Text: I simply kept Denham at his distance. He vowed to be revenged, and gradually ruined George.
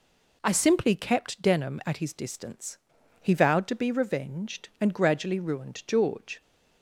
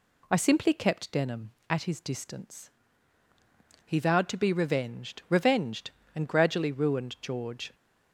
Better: first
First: none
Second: says "revenged" twice; at 5.2 s

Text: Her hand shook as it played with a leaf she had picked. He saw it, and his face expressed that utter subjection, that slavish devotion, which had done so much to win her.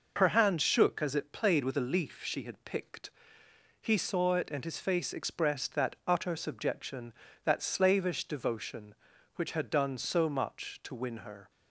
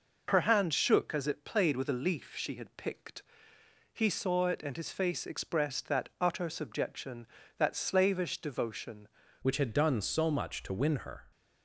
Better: first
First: none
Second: changes voice at "which"; from 9.4 s on; 1.9 s long

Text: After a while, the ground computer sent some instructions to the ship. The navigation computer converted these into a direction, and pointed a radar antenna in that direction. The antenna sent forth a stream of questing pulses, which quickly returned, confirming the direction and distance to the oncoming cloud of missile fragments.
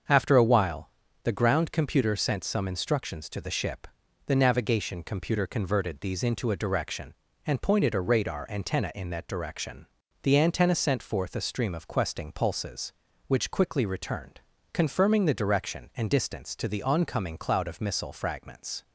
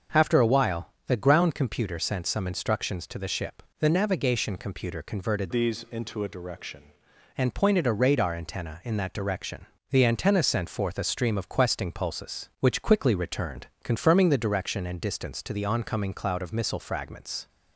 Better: first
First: starts louder than the rest; until 1.4 s; 7 dB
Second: starts louder than the rest; until 1.3 s; 7 dB // changes voice from "these" to "direction"; from 5.5 to 6.8 s; 1.3 s long

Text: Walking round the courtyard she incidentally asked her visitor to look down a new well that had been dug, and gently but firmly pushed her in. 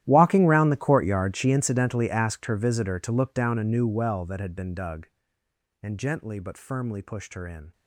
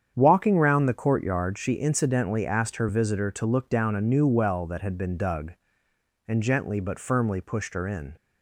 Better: second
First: gets quieter; strong; throughout; 19.5 dB // starts louder than the rest; strong; until 1.0 s; 13 dB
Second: starts louder than the rest; strong; until 1.1 s; 8.5 dB

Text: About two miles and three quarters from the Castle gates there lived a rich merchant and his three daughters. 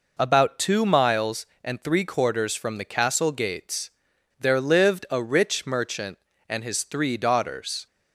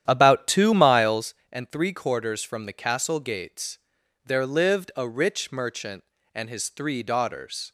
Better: first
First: pauses between "gates" and "there"; noticeable; at 3.8 s; 0.48 s long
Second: starts louder than the rest; strong; until 1.4 s; 10.5 dB // pauses between "gates" and "there"; noticeable; at 3.7 s; 0.46 s long

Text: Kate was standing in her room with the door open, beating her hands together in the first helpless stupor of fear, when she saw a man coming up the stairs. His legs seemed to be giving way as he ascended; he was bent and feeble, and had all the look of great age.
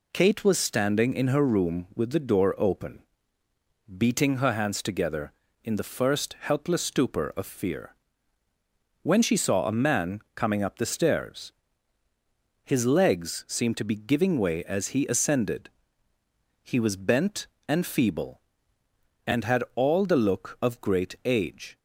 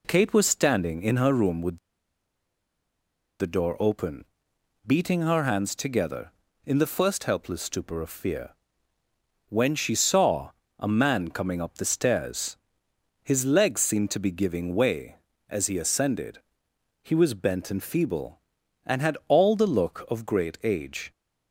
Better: first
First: none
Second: pauses between "with" and "the"; strong; at 1.7 s; 1.6 s long // pauses between "saw" and "a"; slight; at 10.5 s; 0.28 s long

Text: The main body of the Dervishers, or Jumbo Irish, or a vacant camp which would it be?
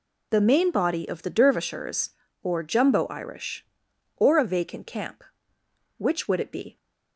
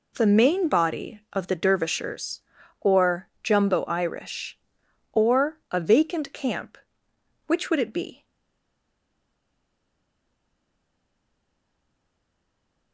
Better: first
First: none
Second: stays silent after the last word; strong; from 8.2 s on; 4.7 s long

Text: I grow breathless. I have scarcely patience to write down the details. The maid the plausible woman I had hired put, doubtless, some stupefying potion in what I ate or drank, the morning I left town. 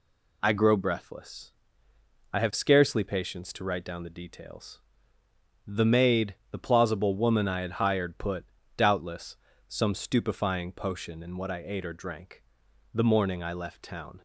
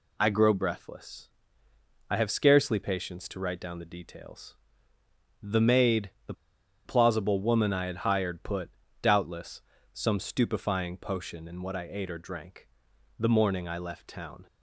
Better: first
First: pauses between "maid" and "the"; slight; at 6.3 s; 0.16 s long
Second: pauses between "maid" and "the"; slight; at 6.0 s; 0.16 s long // pauses between "the" and "plausible"; noticeable; at 6.3 s; 0.52 s long

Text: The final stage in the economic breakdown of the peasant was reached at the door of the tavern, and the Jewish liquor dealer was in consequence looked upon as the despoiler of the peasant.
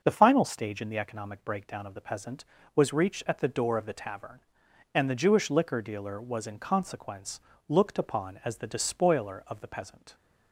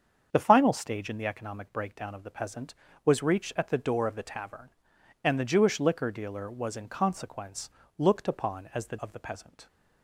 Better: first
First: starts louder than the rest; noticeable; until 1.0 s; 6 dB // pauses between "consequence" and "looked"; slight; at 7.4 s; 0.26 s long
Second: starts louder than the rest; strong; until 1.3 s; 7 dB // pauses between "consequence" and "looked"; slight; at 7.7 s; 0.26 s long // skips "despoiler"; at 8.9 s

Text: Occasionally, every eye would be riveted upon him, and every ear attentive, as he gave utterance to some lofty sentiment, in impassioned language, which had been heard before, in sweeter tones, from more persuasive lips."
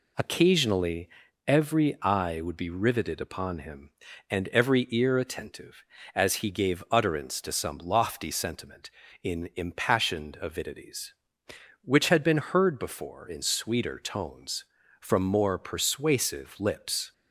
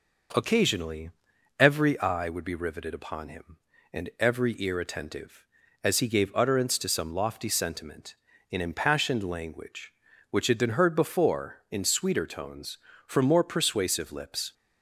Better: second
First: says "avidities" for "language"; at 10.4 s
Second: none

